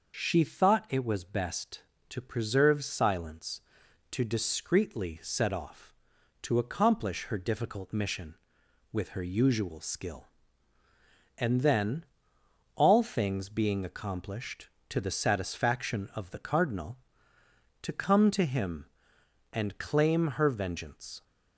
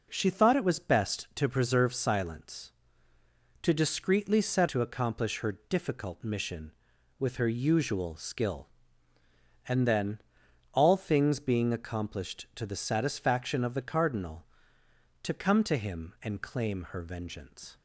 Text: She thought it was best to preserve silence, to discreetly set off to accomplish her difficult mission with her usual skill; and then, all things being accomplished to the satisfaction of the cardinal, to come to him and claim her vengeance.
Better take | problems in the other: first | skips "off"; at 4.6 s

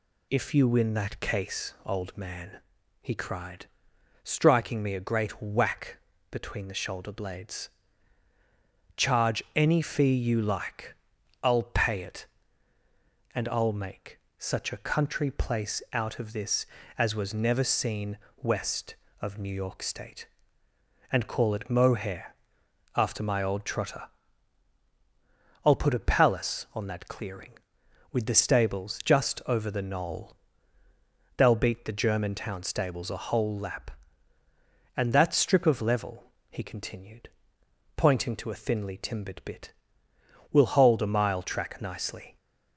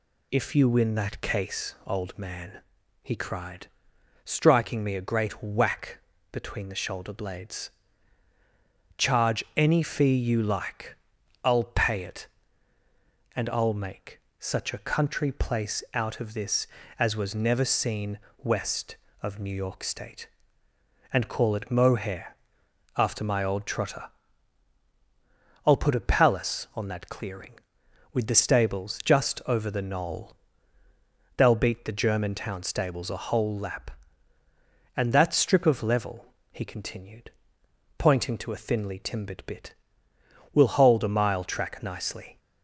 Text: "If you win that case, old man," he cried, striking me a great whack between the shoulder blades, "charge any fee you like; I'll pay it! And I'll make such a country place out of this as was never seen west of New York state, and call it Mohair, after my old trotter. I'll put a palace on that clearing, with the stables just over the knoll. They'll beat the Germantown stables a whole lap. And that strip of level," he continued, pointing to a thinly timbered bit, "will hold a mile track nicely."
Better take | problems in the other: neither | pauses between "whack" and "between"; slight; the same in both // pauses between "make" and "such"; slight; the same in both // pauses between "seen" and "west"; slight; the same in both

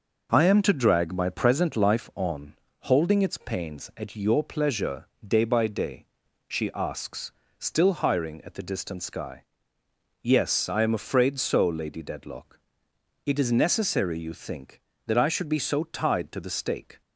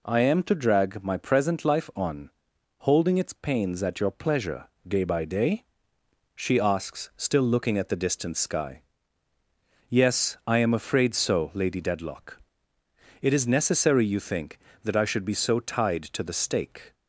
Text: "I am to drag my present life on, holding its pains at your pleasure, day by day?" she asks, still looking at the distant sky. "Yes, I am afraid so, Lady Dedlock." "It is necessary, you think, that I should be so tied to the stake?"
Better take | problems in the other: second | says "hiring" for "looking"; at 7.9 s

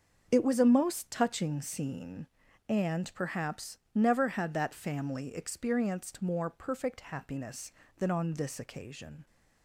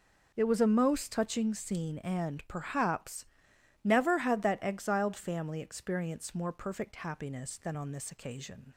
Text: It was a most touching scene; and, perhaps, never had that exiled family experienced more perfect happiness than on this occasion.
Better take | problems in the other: second | starts louder than the rest; until 1.3 s; 6.5 dB // skips "exiled"; at 4.7 s

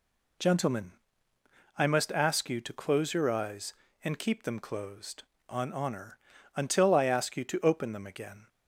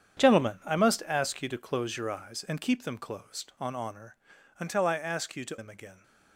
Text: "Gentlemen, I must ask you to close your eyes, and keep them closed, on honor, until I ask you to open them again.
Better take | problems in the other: first | starts louder than the rest; strong; until 1.2 s; 8.5 dB // skips "open"; at 5.5 s

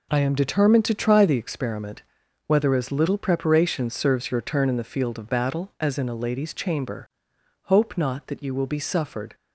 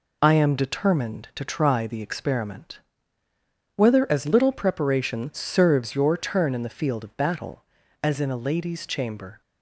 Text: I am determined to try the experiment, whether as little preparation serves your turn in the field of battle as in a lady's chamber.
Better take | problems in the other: second | goes on to say "Hope not that you will be suffered"; strong; from 7.6 s on; 1.7 s long

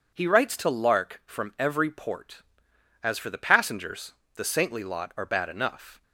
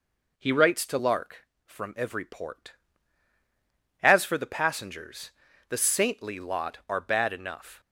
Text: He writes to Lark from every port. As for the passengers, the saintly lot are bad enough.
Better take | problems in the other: neither | none

